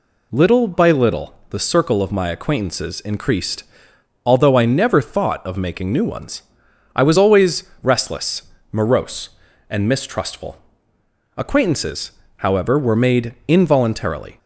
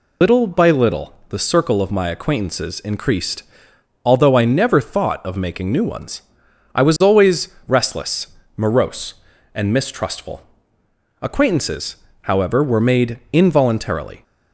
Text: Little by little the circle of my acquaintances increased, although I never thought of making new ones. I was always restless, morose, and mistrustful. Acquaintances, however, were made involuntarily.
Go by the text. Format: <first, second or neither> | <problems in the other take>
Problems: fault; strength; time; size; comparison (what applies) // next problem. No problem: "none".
first | loses the start of "Little"; at 0.2 s; 100 ms // pauses between "little" and "the"; slight; at 1.1 s; 0.16 s long; slight in the first // pauses between "always" and "restless"; slight; at 7.4 s; 0.22 s long; slight in the first